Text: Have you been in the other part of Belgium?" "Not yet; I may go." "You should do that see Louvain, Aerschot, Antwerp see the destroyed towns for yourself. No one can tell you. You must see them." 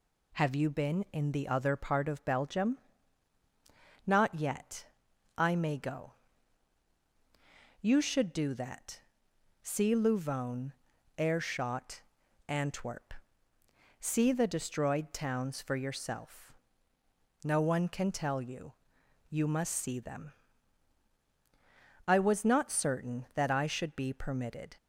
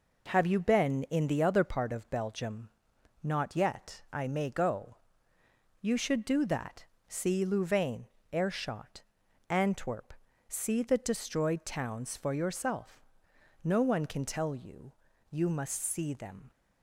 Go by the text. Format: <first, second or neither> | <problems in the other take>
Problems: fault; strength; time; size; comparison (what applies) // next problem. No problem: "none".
second | pauses between "that" and "see"; noticeable; at 8.9 s; 0.64 s long; slight in the second // pauses between "Antwerp" and "see"; noticeable; at 13.1 s; 0.88 s long; slight in the second // goes on to say "I was not certain that I should be permitted"; strong; from 22.0 s on; 2.7 s long